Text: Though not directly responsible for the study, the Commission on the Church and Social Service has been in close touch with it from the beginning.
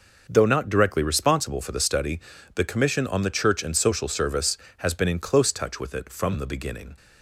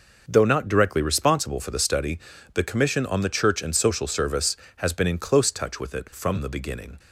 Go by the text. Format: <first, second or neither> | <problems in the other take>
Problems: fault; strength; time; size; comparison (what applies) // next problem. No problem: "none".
neither | none